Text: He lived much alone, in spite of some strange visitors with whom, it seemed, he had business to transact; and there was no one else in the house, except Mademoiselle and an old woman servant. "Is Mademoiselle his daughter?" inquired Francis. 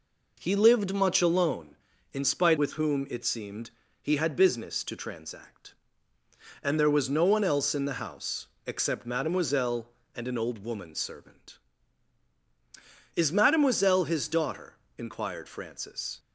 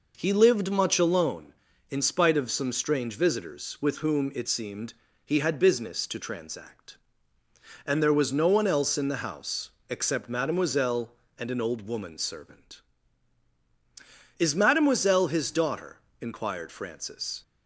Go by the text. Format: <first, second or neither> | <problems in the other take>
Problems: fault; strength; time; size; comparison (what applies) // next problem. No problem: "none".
second | skips "of some strange visitors"; at 2.5 s